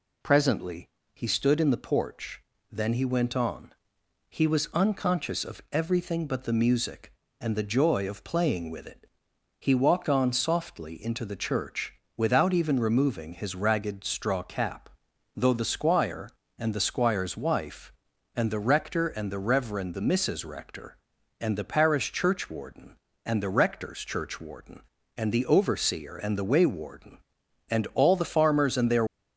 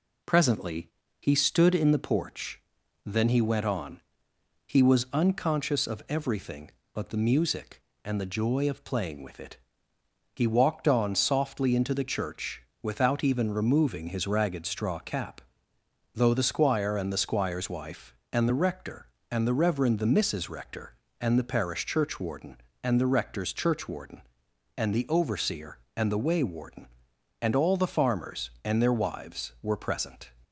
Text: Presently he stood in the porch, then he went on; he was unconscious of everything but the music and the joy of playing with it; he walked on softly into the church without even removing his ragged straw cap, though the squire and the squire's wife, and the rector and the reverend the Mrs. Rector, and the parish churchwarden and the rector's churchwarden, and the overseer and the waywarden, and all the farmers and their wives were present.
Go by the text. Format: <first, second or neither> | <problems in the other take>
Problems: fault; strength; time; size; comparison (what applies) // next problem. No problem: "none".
second | pauses between "Presently" and "he"; slight; at 0.8 s; 0.24 s long; slight in the second // pauses between "church" and "without"; slight; at 11.9 s; 0.22 s long; slight in the second // stops before "wives were present"; at 29.0 s